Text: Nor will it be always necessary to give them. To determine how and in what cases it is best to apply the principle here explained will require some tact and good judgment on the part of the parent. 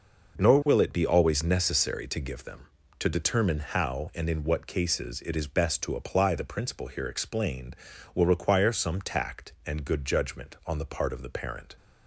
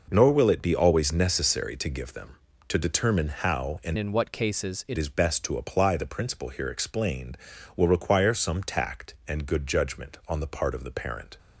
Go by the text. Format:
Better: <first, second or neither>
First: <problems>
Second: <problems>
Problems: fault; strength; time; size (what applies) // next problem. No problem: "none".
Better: first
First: none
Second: changes voice from "in" to "it"; from 3.9 to 4.9 s; 1.0 s long